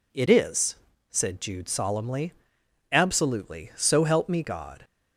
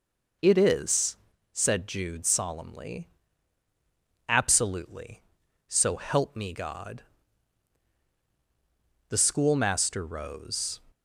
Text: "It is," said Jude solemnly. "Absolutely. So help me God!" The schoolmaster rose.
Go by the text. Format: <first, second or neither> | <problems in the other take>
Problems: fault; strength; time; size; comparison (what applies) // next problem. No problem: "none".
second | stops before "The schoolmaster rose"; at 4.8 s